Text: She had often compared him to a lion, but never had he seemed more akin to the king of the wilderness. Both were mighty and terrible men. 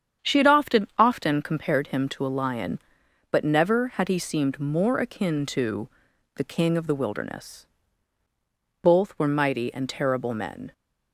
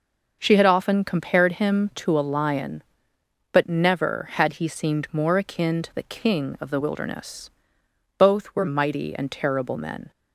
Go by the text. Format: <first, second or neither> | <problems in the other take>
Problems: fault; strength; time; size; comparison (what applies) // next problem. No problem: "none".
second | starts louder than the rest; strong; until 1.3 s; 8 dB // says "often" twice; at 0.9 s // pauses between "to" and "the"; noticeable; at 5.8 s; 0.46 s long